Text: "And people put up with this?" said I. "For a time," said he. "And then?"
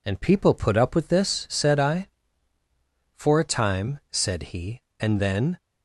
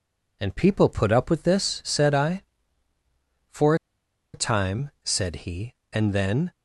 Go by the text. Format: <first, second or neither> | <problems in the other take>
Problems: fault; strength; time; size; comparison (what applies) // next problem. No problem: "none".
first | pauses between "For" and "a"; noticeable; at 3.7 s; 0.59 s long